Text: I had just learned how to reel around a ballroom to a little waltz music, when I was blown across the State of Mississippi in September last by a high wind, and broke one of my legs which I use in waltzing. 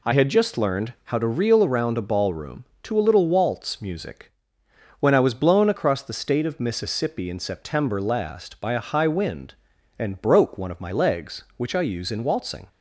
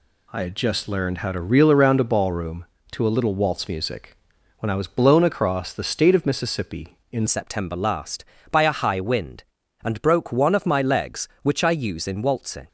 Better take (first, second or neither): first